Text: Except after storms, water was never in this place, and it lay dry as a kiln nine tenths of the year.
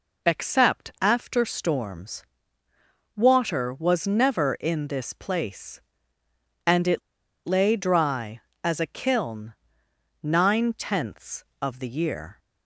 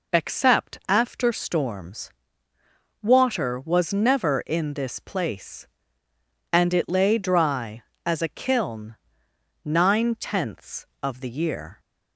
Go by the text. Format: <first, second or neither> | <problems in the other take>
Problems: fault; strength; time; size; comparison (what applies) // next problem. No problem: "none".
second | pauses between "it" and "lay"; at 7.0 s; 0.45 s long // pauses between "kiln" and "nine"; noticeable; at 9.5 s; 0.72 s long; noticeable in the second